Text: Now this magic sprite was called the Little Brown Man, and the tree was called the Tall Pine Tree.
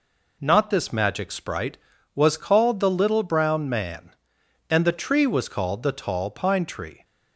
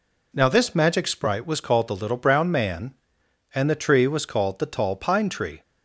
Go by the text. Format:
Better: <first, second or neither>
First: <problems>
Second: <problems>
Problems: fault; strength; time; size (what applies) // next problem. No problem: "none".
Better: second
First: says "Not" for "Now"; at 0.4 s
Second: none